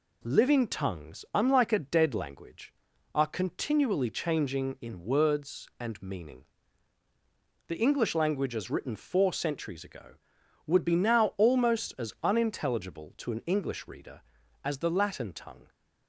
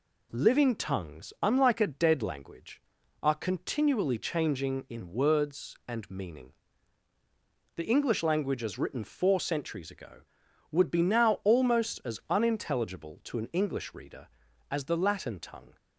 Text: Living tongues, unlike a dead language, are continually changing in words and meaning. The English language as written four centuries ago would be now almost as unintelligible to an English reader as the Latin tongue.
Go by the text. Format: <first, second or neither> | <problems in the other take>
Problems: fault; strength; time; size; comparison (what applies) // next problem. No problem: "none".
neither | none